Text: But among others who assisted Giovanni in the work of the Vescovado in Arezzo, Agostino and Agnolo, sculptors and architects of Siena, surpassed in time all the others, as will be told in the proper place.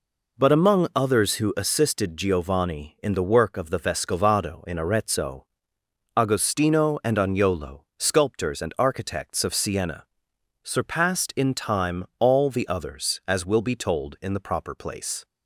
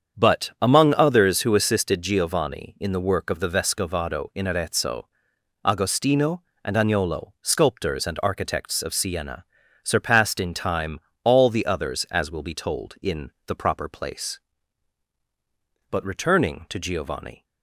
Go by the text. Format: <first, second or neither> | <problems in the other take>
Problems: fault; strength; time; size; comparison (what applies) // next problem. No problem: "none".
first | starts louder than the rest; strong; until 1.2 s; 7.5 dB // pauses between "time" and "all"; slight; at 10.9 s; 0.24 s long // pauses between "in" and "the"; slight; at 13.3 s; 0.16 s long // goes on to say "But returning to Giovanni"; from 15.8 s on; 1.5 s long